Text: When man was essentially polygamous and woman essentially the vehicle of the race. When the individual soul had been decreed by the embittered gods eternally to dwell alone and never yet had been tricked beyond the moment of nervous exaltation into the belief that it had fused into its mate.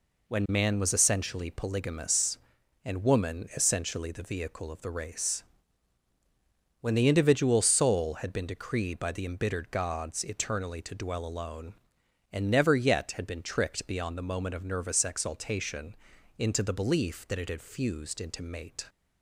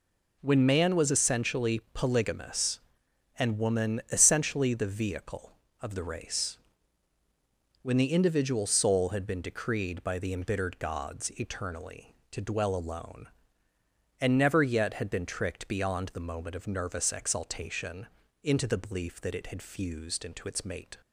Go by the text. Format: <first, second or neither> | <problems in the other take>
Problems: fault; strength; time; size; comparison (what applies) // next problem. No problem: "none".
second | pauses between "exaltation" and "into"; at 15.9 s; 0.42 s long; also in the second // skips "its"; at 18.4 s